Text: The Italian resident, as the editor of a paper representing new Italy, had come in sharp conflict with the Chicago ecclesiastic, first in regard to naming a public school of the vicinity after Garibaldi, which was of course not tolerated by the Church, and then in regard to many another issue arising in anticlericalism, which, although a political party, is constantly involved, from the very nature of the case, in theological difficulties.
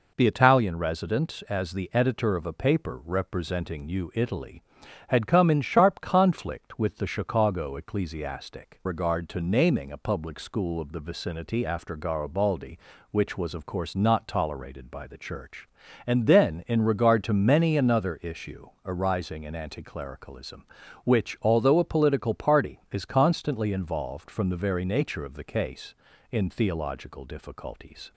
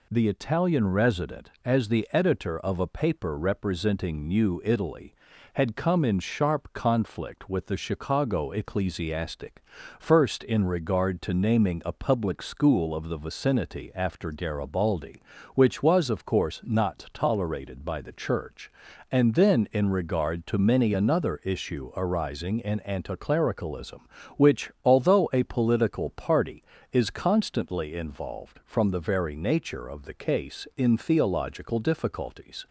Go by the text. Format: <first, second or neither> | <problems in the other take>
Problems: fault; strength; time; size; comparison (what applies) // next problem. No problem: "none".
second | skips "first in"; at 8.8 s // pauses between "issue" and "arising"; slight; at 18.6 s; 0.16 s long